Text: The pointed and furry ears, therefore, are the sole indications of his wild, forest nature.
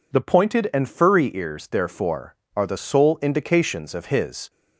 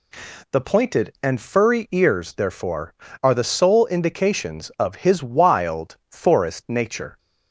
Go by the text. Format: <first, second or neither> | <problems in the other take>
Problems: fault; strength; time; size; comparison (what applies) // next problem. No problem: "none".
second | stops before "wild forest nature"; at 4.4 s